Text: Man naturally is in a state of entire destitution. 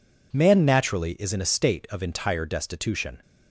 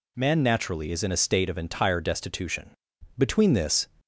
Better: first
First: none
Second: goes on to say "Between this"; noticeable; from 3.1 s on; 0.70 s long

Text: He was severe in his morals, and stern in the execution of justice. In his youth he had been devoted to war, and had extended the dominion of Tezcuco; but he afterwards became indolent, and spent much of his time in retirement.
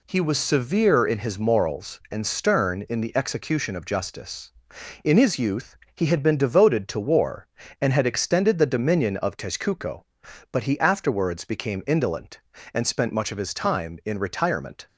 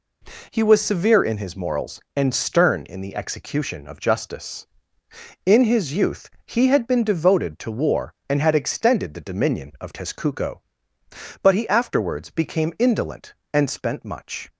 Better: first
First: pauses between "youth" and "he"; slight; at 5.7 s; 0.18 s long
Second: pauses between "youth" and "he"; slight; at 6.2 s; 0.18 s long // stops before "of his time in retirement"; at 14.4 s

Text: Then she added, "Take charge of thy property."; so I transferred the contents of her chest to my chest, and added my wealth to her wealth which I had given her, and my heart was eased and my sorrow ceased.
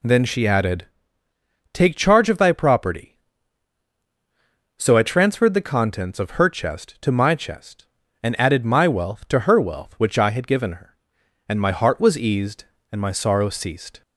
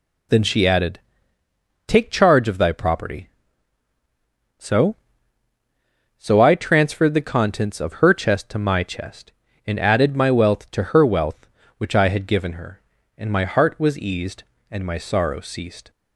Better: first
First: none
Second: says "so" twice; at 6.1 s

